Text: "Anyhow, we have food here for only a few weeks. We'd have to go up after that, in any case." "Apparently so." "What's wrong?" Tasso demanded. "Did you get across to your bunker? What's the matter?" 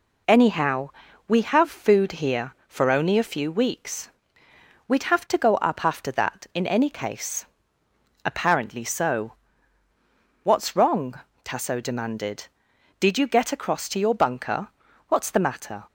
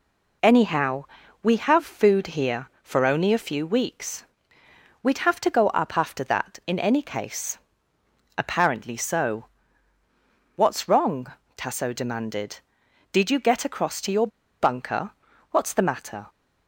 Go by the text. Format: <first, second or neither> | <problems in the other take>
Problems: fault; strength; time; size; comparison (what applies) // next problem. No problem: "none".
first | pauses between "your" and "bunker"; slight; at 14.2 s; 0.33 s long